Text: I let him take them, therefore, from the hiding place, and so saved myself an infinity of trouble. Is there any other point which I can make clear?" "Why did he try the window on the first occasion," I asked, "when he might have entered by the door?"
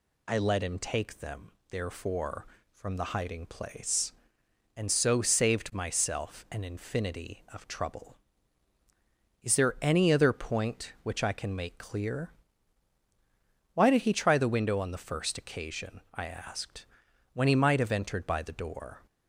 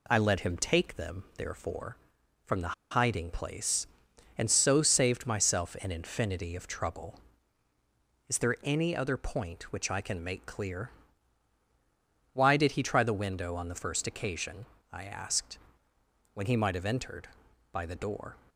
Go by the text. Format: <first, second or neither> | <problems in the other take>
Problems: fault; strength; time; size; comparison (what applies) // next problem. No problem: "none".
first | pauses between "the" and "hiding"; slight; at 2.7 s; 0.19 s long